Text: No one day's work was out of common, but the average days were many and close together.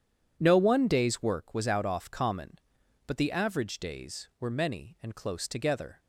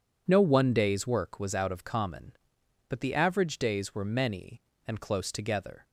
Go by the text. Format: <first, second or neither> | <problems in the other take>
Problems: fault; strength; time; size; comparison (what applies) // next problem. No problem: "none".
second | starts louder than the rest; strong; until 1.3 s; 9 dB // says "off" for "of"; at 1.8 s